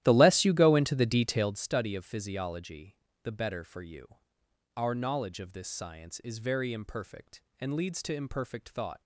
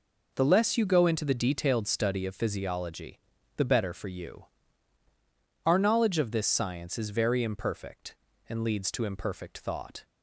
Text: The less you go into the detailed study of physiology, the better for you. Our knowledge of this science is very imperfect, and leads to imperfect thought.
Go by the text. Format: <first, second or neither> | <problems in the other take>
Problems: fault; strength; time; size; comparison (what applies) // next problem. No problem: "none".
second | starts louder than the rest; strong; until 1.7 s; 13.5 dB